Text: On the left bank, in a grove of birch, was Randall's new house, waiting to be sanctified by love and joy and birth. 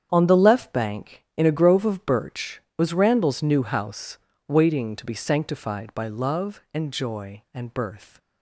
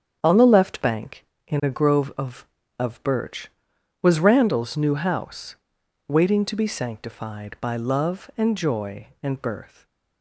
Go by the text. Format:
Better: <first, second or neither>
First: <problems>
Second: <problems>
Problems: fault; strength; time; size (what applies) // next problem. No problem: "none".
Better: first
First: starts louder than the rest; strong; until 1.1 s; 8 dB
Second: starts louder than the rest; strong; until 1.2 s; 8 dB // says "of" twice; at 2.7 s // stays silent after the last word; slight; from 9.6 s on; 0.6 s long